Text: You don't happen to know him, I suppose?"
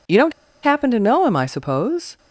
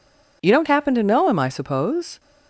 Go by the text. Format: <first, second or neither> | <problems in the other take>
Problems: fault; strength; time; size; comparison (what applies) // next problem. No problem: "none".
second | pauses between "don't" and "happen"; slight; at 0.3 s; 0.30 s long